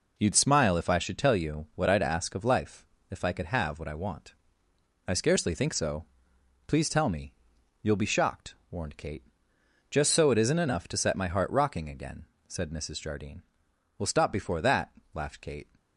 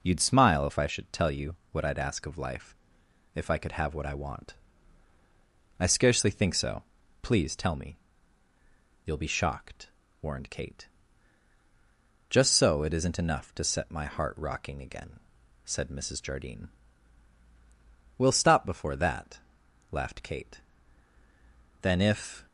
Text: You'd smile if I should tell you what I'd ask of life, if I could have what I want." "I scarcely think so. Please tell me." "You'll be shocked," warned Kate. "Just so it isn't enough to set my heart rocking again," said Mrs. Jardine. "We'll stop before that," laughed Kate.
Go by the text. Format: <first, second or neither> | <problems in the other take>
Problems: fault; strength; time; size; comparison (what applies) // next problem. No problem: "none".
first | pauses between "you" and "what"; slight; at 1.5 s; 0.18 s long // goes on to say "Then if"; noticeable; from 21.8 s on; 0.64 s long